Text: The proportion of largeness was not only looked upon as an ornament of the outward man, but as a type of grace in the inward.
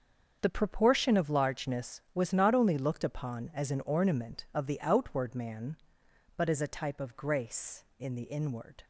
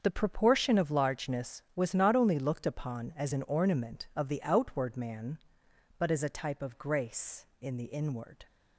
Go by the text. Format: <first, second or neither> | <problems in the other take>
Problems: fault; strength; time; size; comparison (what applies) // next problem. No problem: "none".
neither | starts louder than the rest; the same in both